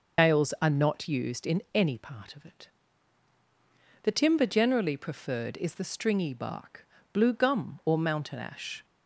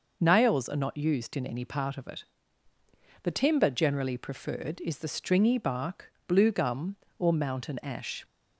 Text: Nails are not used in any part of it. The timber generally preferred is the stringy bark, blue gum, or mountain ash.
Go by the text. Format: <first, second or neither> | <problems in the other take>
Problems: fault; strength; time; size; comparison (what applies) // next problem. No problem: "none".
second | loses the start of "Nails"; at 0.1 s; 115 ms